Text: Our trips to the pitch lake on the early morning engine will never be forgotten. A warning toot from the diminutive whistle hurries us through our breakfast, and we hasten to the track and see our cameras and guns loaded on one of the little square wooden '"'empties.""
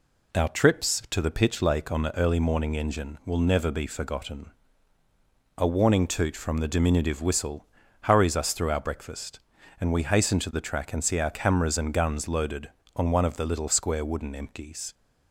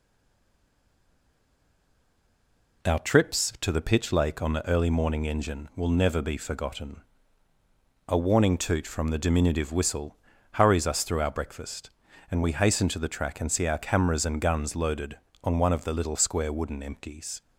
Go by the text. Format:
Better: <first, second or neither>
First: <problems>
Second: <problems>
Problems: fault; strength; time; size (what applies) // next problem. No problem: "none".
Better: first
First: pauses between "whistle" and "hurries"; slight; at 7.6 s; 0.36 s long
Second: stays silent before the first word; strong; until 2.8 s; 2.8 s long // pauses between "whistle" and "hurries"; slight; at 10.1 s; 0.36 s long